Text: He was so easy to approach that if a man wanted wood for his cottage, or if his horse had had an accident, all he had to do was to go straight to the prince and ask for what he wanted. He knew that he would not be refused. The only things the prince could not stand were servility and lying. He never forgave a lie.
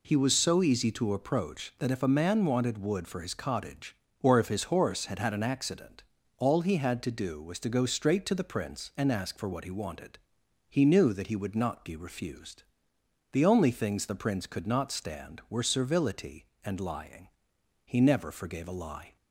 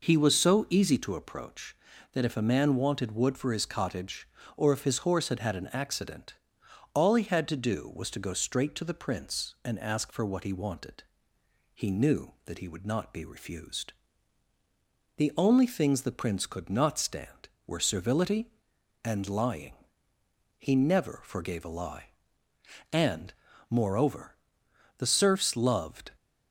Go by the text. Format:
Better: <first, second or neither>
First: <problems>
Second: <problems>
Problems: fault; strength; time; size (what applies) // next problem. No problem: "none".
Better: first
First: none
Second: goes on to say "And moreover the serfs loved"; strong; from 22.9 s on; 3.2 s long